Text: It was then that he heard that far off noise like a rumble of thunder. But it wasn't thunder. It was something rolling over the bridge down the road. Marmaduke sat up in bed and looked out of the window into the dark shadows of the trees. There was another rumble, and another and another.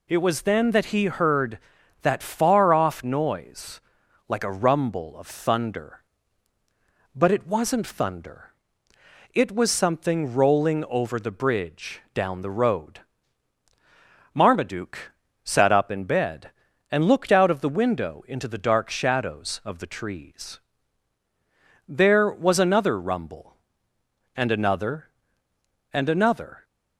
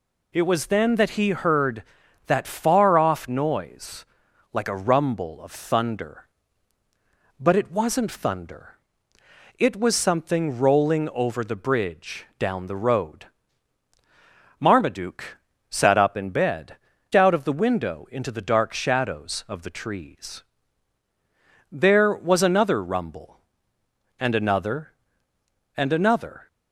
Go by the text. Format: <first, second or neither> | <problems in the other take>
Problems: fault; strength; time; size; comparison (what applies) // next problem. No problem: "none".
first | pauses between "noise" and "like"; noticeable; at 4.0 s; 0.48 s long; noticeable in the first // pauses between "Marmaduke" and "sat"; slight; at 15.3 s; 0.32 s long; slight in the first // skips "and looked"; at 16.9 s